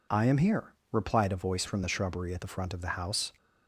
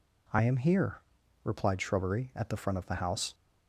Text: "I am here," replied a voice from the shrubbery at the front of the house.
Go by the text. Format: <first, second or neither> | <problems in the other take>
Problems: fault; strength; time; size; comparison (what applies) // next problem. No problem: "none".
first | skips "a voice from the"; at 1.7 s